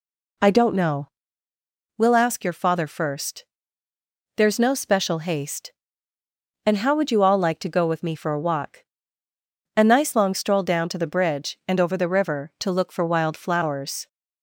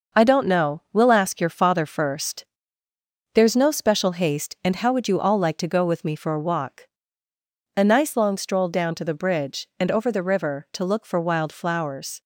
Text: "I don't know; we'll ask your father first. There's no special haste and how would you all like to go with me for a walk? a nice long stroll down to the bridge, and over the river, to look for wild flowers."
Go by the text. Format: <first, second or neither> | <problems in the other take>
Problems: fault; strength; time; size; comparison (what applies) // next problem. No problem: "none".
first | gets quieter; noticeable; throughout; 5.5 dB